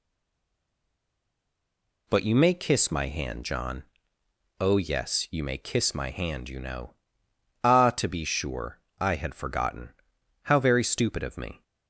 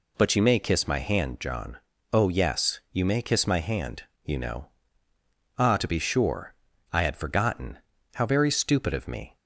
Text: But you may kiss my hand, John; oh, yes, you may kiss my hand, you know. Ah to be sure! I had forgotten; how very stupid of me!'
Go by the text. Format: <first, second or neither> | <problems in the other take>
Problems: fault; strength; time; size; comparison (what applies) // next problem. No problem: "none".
second | stays silent before the first word; noticeable; until 2.0 s; 2.0 s long